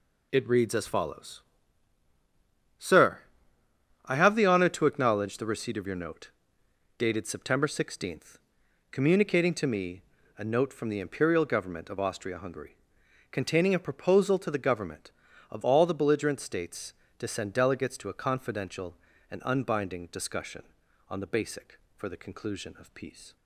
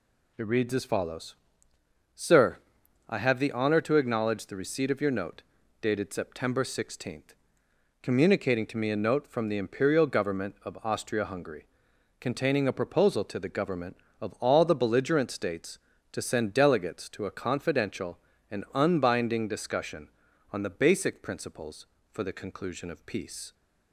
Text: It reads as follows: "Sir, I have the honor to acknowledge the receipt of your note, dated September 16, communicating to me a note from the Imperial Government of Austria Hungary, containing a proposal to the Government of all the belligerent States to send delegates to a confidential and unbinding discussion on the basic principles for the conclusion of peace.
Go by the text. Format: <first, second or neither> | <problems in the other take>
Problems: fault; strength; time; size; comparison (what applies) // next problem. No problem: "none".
second | pauses between "me" and "a"; slight; at 10.0 s; 0.34 s long // skips "principles"; at 21.8 s